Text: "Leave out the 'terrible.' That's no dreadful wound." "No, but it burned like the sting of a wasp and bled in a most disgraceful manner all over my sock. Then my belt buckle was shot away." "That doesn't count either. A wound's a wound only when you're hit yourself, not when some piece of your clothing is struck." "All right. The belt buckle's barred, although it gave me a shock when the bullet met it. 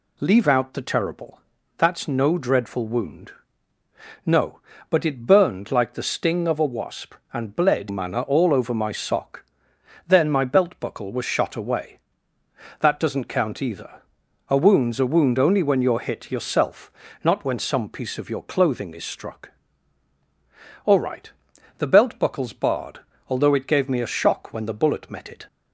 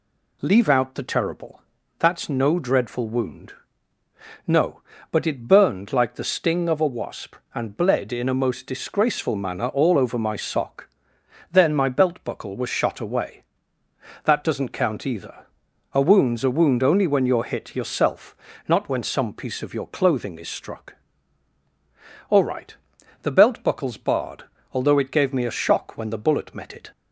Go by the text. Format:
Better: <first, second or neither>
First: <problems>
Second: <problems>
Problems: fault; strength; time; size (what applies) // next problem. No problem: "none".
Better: second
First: skips "in a most disgraceful"; at 7.8 s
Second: none